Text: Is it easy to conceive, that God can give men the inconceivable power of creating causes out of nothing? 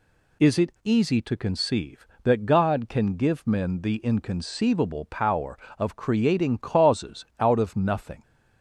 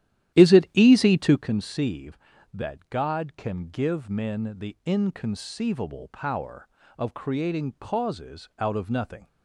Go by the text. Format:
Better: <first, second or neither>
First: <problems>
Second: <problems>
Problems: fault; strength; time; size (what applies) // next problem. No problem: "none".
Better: first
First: none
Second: starts louder than the rest; strong; until 1.5 s; 12 dB